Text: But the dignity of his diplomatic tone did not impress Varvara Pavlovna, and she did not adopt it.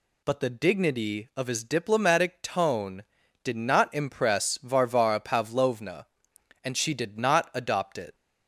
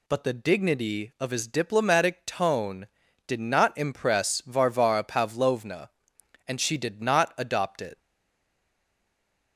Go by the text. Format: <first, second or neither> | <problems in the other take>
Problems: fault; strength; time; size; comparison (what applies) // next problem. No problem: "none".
first | stays silent after the last word; noticeable; from 7.9 s on; 1.6 s long